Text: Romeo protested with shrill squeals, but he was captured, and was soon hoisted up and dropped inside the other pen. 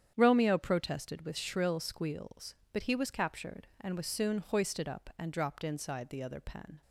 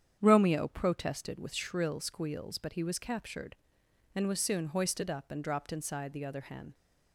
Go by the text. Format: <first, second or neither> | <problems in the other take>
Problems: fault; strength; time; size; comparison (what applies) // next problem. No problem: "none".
first | starts louder than the rest; strong; until 1.2 s; 8.5 dB; strong in the first // says "hen" for "pen"; at 6.4 s